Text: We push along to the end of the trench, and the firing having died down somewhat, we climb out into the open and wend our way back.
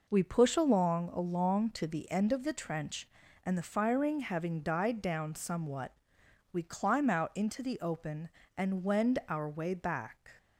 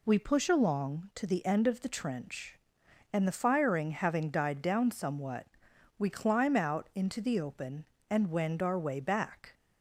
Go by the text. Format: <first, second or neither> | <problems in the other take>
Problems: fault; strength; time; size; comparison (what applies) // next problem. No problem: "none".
second | says "along" twice; at 1.0 s